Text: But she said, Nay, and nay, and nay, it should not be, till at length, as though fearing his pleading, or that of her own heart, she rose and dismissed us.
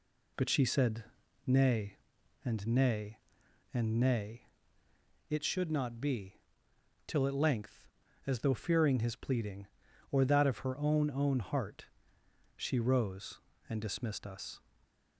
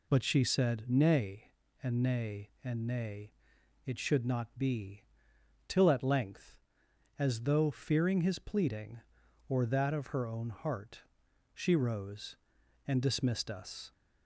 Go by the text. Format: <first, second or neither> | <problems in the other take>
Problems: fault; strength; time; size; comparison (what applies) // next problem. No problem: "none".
second | says "own" twice; at 11.0 s